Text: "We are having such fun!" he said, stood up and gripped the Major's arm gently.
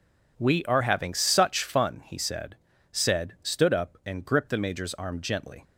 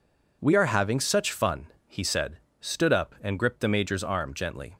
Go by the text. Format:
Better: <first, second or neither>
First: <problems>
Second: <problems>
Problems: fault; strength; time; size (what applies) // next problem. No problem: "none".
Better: second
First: says "said" twice; at 2.9 s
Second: none